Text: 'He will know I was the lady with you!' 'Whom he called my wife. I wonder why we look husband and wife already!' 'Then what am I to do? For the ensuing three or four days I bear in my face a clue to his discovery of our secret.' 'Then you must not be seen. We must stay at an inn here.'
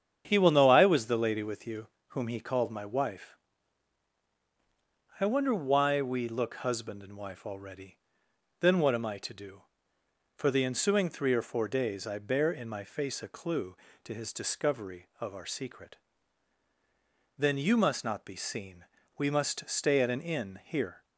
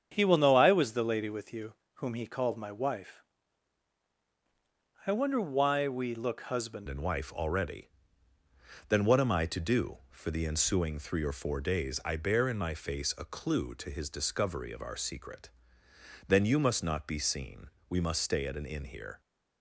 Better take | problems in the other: first | starts louder than the rest; strong; until 1.1 s; 8 dB; strong in the first // changes voice at "and"; from 6.8 s on; 12.4 s long

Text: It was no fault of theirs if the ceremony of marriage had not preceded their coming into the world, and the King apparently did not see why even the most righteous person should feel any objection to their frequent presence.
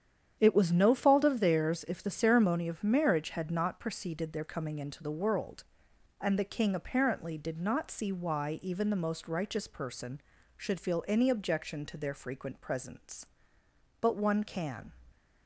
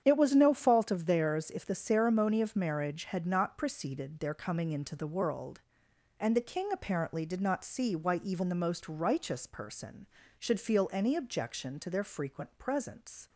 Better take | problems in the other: second | starts louder than the rest; strong; until 1.4 s; 9 dB; strong in the second // goes on to say "But one can"; noticeable; from 13.9 s on; 0.92 s long

